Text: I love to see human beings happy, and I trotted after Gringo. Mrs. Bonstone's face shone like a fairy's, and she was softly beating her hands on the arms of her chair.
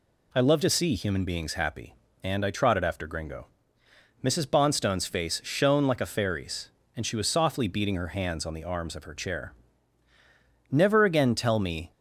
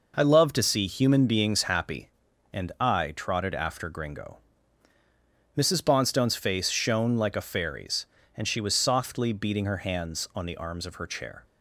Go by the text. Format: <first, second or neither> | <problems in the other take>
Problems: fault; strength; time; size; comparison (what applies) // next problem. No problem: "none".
second | goes on to say "Never again tell me"; noticeable; from 10.7 s on; 1.2 s long